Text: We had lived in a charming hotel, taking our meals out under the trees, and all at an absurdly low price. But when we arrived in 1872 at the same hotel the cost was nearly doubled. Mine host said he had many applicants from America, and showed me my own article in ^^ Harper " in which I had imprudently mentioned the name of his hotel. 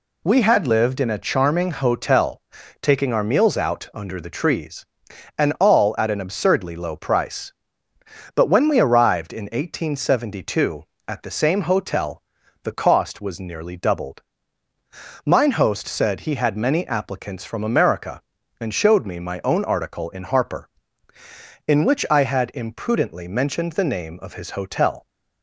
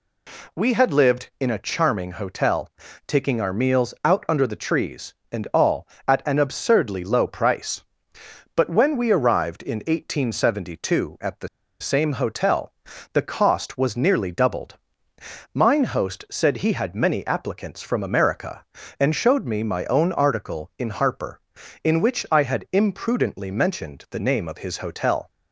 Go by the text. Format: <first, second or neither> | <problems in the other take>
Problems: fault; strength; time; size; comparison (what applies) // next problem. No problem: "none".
first | pauses between "the" and "same"; slight; at 11.4 s; 0.32 s long // pauses between "hotel" and "the"; at 12.7 s; 0.40 s long; also in the first